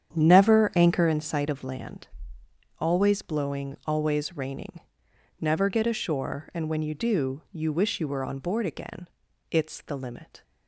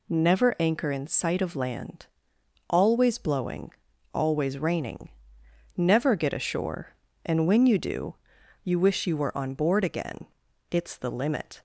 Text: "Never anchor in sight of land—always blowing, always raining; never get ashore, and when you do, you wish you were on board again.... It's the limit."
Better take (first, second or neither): second